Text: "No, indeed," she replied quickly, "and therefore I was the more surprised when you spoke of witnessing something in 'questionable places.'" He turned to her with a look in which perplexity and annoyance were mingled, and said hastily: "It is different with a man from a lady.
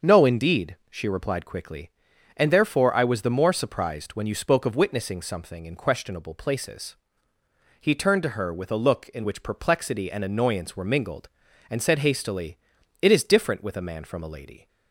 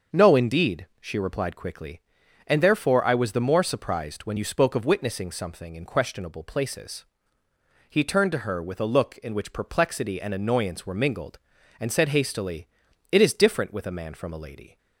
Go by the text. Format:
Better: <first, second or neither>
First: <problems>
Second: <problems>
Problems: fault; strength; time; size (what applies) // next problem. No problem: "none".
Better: neither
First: starts louder than the rest; until 1.1 s; 6.5 dB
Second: starts louder than the rest; until 1.2 s; 6.5 dB